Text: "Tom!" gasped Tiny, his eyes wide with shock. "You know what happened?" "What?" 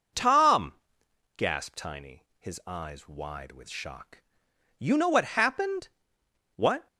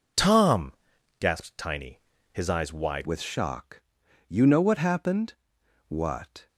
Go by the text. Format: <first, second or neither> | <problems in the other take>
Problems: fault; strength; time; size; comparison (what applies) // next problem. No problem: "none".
first | changes voice at "with"; from 3.0 s on; 3.4 s long